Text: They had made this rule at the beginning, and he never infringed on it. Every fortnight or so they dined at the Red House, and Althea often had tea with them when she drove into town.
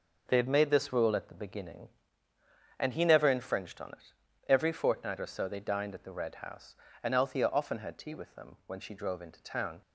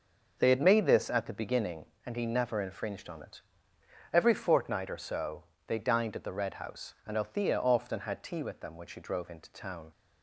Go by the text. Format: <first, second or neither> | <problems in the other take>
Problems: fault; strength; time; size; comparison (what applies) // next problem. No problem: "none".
first | starts louder than the rest; until 1.3 s; 6 dB // skips "rule"; at 1.1 s // pauses between "so" and "they"; slight; at 5.4 s; 0.24 s long